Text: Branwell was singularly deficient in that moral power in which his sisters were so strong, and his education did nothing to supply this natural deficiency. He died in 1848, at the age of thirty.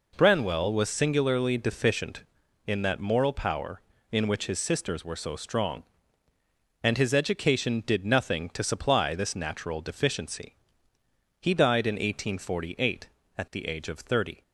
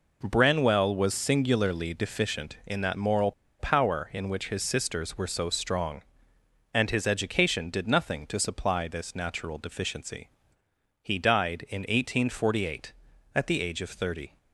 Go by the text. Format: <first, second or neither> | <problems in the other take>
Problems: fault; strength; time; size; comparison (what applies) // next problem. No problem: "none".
first | pauses between "moral" and "power"; slight; at 3.3 s; 0.27 s long